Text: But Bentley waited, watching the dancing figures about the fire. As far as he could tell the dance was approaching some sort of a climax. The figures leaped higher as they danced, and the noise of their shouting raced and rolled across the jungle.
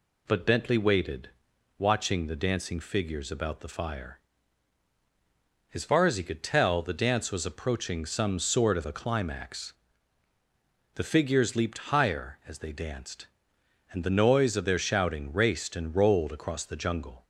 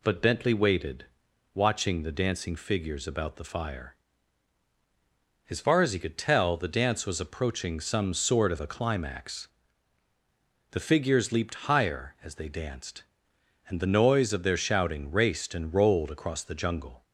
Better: neither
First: none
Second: none

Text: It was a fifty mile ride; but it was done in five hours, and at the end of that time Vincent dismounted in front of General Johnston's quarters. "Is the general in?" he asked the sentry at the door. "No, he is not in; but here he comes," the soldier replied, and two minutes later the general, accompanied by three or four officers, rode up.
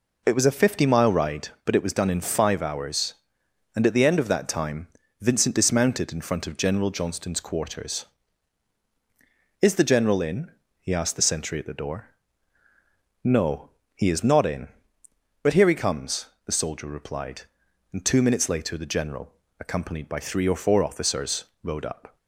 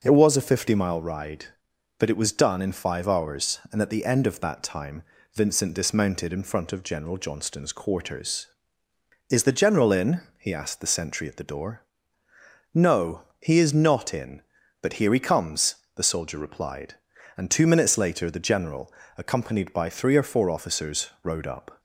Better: neither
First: pauses between "time" and "Vincent"; slight; at 4.8 s; 0.32 s long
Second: pauses between "time" and "Vincent"; slight; at 5.0 s; 0.30 s long

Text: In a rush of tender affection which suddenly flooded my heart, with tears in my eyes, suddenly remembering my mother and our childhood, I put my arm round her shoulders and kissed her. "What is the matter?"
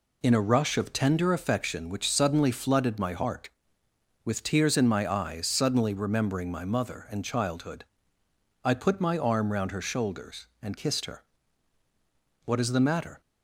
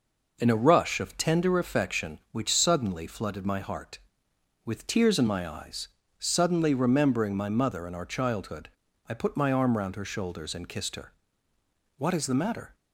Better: second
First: skips "our"; at 7.2 s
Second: none

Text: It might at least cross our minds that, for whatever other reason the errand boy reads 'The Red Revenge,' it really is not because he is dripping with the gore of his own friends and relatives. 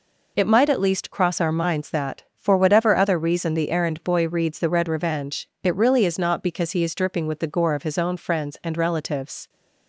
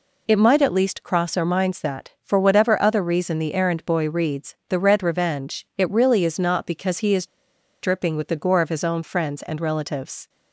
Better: first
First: none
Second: pauses between "is" and "dripping"; noticeable; at 7.2 s; 0.53 s long

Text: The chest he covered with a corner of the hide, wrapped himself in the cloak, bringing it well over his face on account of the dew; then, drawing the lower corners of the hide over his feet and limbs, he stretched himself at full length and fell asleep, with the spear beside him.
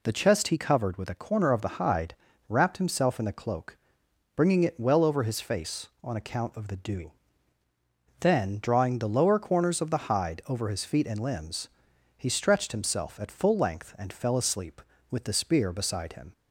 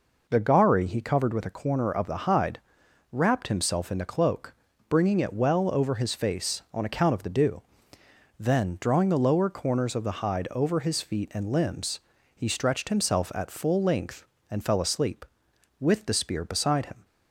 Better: first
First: none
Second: says "gari" for "chest"; at 0.4 s

